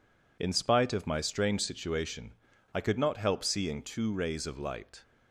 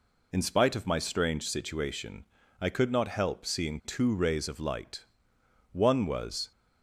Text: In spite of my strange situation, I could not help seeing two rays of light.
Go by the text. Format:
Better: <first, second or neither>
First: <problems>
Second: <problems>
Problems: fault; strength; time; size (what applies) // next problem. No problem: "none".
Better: first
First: none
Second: goes on to say "One was"; noticeable; from 5.7 s on; 0.78 s long